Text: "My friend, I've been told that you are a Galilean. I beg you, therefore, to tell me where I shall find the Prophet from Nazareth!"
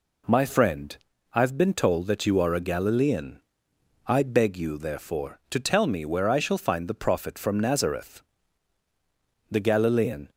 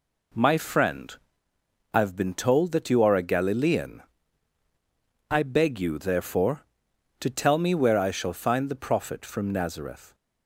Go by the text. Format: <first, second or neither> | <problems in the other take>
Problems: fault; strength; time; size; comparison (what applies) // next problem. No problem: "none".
second | goes on to say "The Galilean"; noticeable; from 9.5 s on; 0.78 s long